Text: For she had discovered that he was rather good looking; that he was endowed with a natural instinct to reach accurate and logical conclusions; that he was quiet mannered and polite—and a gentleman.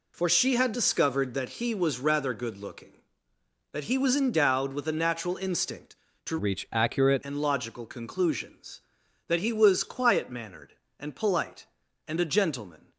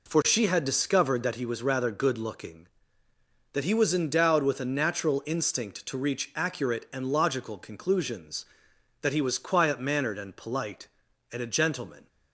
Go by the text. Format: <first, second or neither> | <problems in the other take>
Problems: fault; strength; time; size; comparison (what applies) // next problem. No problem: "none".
second | changes voice from "reach" to "accurate"; from 6.3 to 7.2 s; 0.9 s long